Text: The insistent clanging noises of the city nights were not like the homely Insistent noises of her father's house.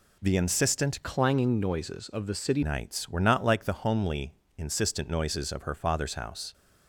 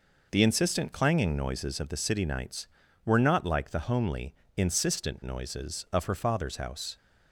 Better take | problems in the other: second | changes voice from "clanging" to "city"; from 1.0 to 2.6 s; 1.6 s long // pauses between "homely" and "Insistent"; slight; at 4.3 s; 0.22 s long; slight in the second

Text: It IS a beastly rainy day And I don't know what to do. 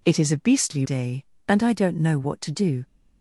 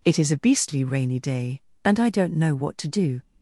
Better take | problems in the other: second | skips "rainy"; at 0.8 s

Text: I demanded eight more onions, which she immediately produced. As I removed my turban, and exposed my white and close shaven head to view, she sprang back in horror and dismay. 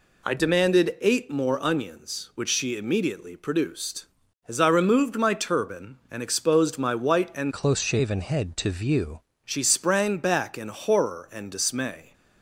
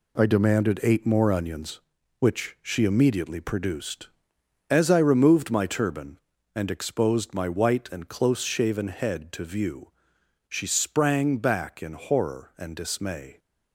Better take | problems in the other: second | changes voice from "close" to "view"; from 7.5 to 9.2 s; 1.7 s long

